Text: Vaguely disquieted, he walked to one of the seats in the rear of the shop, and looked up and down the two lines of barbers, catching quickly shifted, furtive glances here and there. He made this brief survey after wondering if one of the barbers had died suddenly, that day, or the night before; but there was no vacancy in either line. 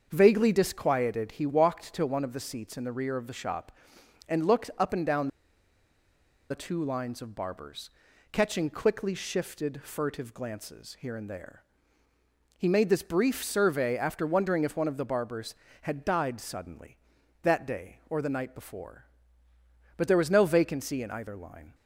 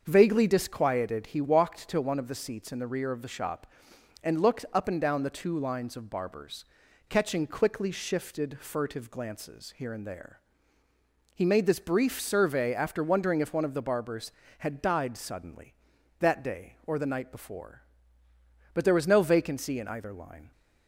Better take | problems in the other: second | starts louder than the rest; until 1.1 s; 6.5 dB; also in the second // pauses between "down" and "the"; at 5.2 s; 1.2 s long

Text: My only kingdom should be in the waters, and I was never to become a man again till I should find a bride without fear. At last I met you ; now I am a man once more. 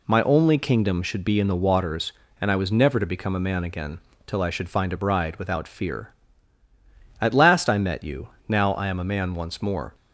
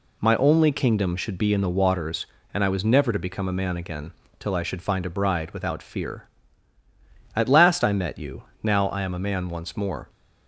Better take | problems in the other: neither | pauses between "again" and "till"; slight; the same in both

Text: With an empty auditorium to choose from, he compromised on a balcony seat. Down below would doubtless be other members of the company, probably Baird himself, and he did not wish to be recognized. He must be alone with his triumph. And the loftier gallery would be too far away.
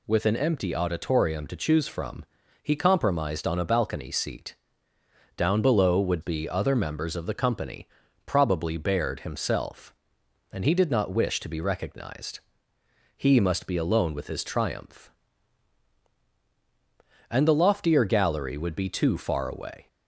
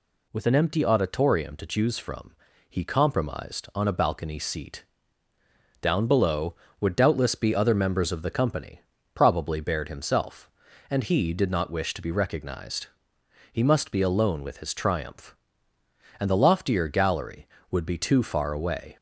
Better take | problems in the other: second | skips "doubtless"; at 6.2 s

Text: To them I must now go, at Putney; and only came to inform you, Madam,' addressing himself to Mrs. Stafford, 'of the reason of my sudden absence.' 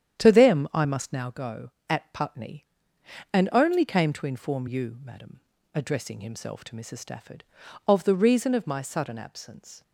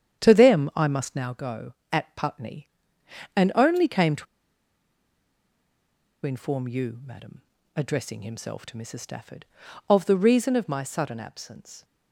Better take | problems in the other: first | starts louder than the rest; strong; until 1.2 s; 9.5 dB; strong in the first // pauses between "to" and "inform"; strong; at 4.2 s; 2.0 s long

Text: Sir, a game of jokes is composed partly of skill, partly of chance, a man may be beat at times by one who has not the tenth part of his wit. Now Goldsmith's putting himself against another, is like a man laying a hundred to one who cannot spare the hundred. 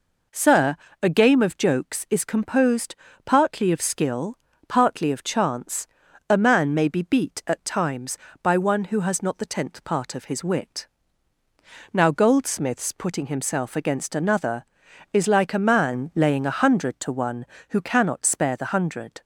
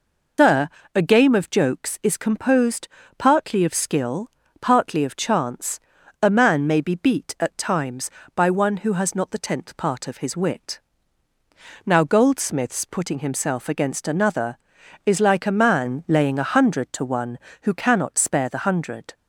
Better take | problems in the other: first | loses the start of "Sir"; at 0.3 s; 150 ms // pauses between "composed" and "partly"; slight; at 2.8 s; 0.30 s long; slight in the first

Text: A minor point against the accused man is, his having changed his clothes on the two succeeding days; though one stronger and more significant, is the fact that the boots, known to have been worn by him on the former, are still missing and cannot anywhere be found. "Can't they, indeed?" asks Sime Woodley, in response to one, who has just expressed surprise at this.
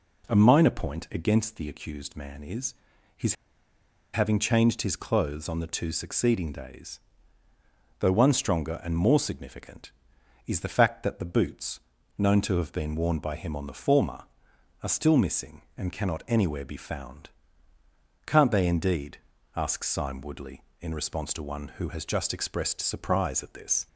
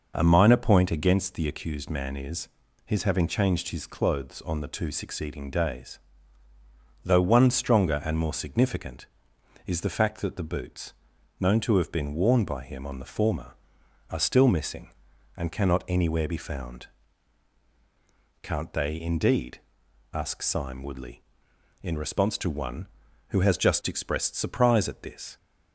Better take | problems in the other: second | pauses between "his" and "having"; noticeable; at 3.3 s; 0.78 s long

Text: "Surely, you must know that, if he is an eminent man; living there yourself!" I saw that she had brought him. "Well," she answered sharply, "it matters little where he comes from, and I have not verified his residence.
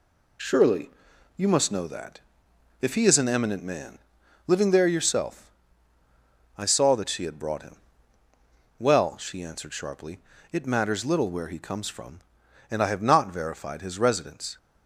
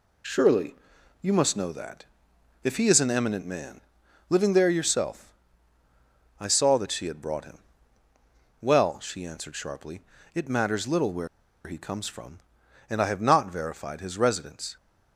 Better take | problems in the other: first | pauses between "where" and "he"; at 11.2 s; 0.38 s long

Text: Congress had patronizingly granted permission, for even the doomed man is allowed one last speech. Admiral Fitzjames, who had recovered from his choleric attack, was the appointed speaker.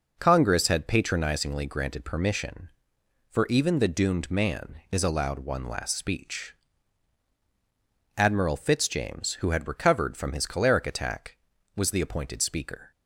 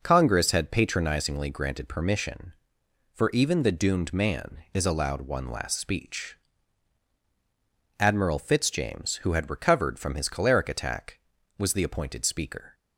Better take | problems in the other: neither | none

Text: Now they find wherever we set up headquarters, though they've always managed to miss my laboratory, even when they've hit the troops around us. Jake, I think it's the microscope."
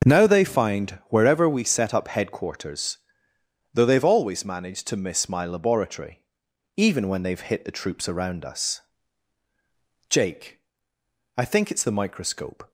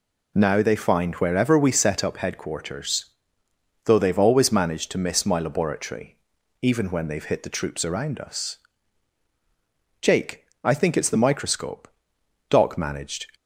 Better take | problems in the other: first | goes on to say "Doc managed"; noticeable; from 12.4 s on; 0.78 s long

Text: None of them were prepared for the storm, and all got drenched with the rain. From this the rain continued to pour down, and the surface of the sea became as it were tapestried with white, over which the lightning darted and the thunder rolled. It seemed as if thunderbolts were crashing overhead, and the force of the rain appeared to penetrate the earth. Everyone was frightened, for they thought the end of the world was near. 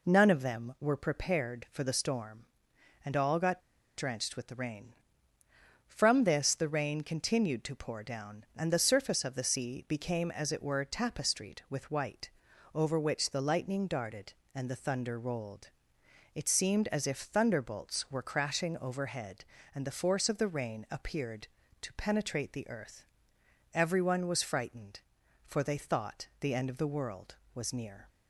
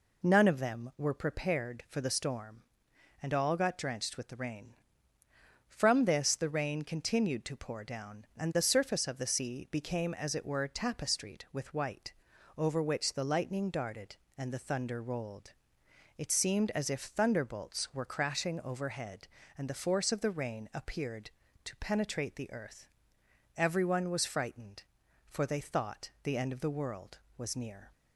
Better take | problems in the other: second | pauses between "got" and "drenched"; at 3.6 s; 0.37 s long

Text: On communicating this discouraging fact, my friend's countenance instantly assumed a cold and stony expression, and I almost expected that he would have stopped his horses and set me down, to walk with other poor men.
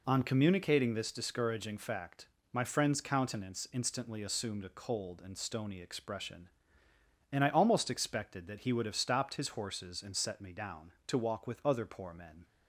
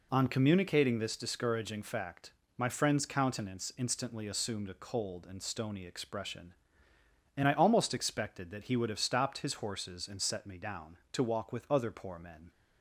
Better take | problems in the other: neither | none

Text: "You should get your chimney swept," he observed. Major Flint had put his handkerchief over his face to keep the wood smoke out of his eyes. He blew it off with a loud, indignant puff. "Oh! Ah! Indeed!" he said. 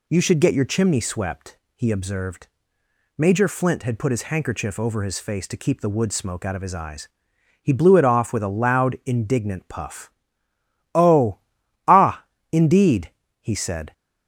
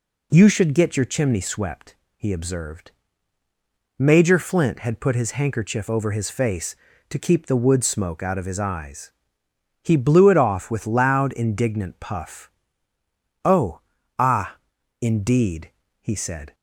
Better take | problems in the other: first | skips "a"; at 10.8 s

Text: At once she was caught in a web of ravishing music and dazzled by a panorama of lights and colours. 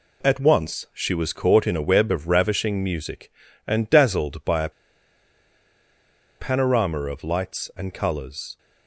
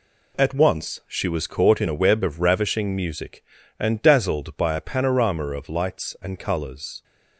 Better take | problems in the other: second | pauses between "a" and "panorama"; strong; at 4.6 s; 1.6 s long

